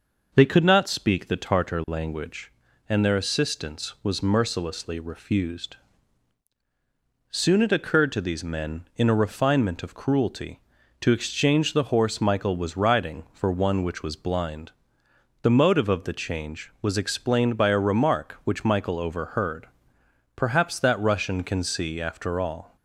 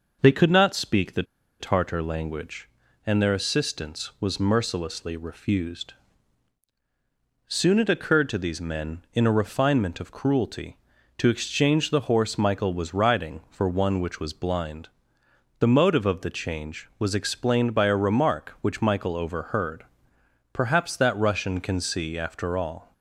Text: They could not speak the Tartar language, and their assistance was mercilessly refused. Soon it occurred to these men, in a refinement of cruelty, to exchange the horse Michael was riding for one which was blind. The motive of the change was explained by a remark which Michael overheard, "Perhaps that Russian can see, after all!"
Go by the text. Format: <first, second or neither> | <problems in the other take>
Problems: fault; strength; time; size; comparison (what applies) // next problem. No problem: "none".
first | pauses between "the" and "Tartar"; at 1.2 s; 0.37 s long